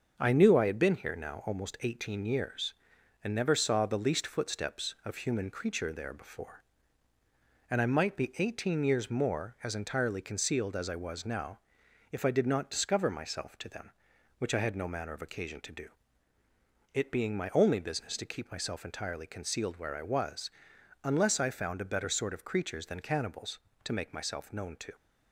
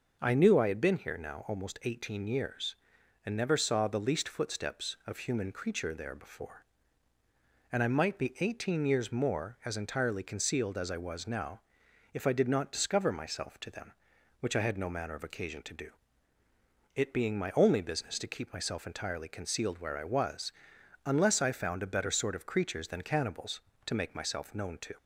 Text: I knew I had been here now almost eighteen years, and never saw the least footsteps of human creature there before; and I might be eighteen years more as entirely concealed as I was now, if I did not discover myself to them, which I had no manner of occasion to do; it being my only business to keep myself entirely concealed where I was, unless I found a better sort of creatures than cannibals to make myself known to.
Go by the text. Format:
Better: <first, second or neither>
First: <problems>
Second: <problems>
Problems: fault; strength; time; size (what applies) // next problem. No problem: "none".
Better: second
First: gets quieter; noticeable; throughout; 4.5 dB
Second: none